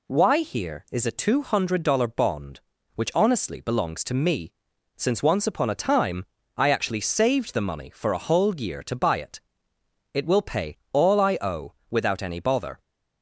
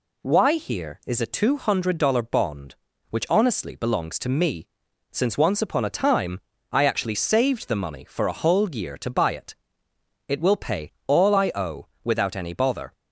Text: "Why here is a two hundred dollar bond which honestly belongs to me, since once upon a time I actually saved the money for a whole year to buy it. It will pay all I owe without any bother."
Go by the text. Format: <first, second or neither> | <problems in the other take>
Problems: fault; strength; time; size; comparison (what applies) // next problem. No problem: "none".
neither | pauses between "time" and "I"; slight; the same in both // pauses between "pay" and "all"; slight; the same in both // pauses between "owe" and "without"; slight; the same in both